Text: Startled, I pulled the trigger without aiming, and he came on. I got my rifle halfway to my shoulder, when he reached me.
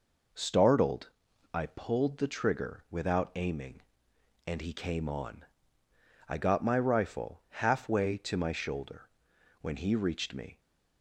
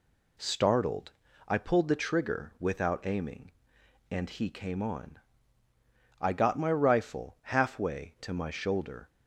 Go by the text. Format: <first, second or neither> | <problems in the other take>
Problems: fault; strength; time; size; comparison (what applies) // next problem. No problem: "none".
first | stops before "when he reached me"; at 9.0 s